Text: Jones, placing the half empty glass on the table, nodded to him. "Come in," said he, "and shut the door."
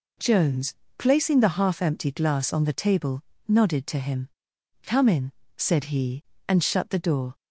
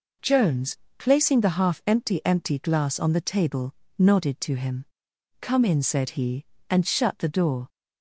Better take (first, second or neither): first